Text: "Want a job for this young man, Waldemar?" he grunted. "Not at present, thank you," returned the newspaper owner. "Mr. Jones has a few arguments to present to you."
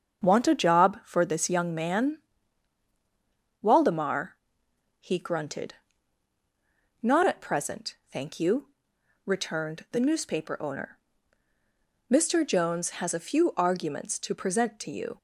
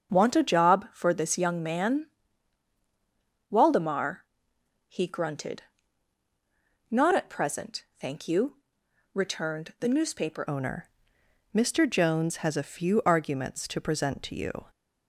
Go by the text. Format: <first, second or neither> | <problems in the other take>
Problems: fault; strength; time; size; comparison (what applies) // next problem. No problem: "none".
first | starts louder than the rest; strong; until 1.1 s; 7 dB; also in the first // changes voice at "owner"; from 10.4 s on; 4.2 s long